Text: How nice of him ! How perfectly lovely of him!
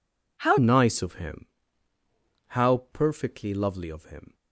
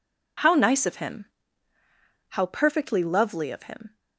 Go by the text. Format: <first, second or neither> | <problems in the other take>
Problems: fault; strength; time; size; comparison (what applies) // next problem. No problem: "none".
second | changes voice at "nice"; from 0.5 s on; 3.8 s long